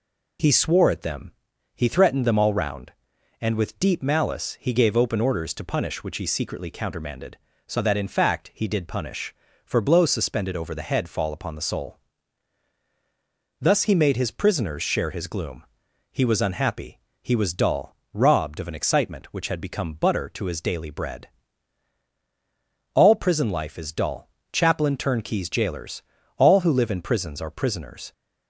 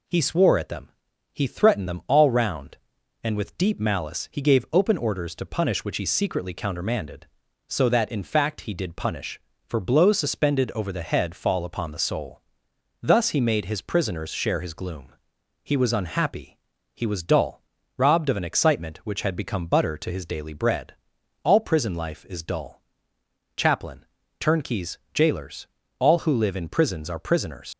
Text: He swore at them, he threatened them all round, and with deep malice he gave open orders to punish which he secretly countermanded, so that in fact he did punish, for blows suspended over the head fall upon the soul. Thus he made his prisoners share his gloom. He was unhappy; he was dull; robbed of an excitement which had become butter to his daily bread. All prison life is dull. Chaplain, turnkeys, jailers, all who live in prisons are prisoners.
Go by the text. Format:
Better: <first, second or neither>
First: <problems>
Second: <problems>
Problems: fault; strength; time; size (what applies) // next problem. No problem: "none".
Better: first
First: none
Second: leaves "prisoners" unfinished; at 27.7 s; 60 ms